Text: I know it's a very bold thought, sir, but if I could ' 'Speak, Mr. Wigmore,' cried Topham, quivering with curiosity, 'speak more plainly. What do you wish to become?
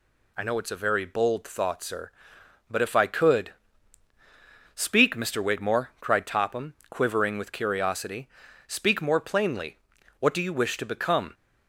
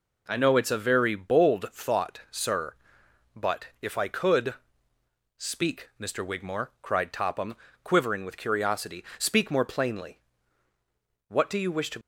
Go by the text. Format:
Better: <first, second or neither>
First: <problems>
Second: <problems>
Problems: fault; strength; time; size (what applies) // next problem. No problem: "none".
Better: first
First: none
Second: stops before "become"; at 12.0 s